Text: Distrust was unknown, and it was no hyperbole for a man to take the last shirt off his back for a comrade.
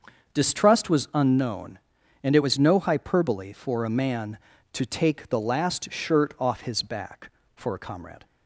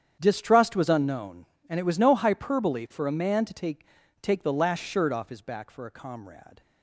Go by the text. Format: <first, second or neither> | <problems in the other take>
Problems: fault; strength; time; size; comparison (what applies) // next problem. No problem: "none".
first | starts louder than the rest; strong; until 1.2 s; 8.5 dB; also in the first // says "take" twice; at 4.2 s